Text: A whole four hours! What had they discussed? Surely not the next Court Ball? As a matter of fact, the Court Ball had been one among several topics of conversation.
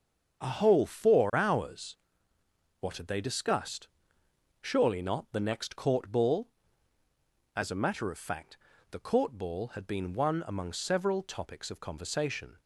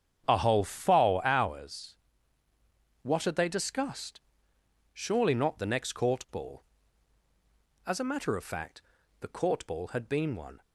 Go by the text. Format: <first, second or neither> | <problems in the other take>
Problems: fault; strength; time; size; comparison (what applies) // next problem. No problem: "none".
first | starts louder than the rest; strong; until 1.2 s; 8 dB; also in the first // stops before "among several topics of conversation"; at 10.6 s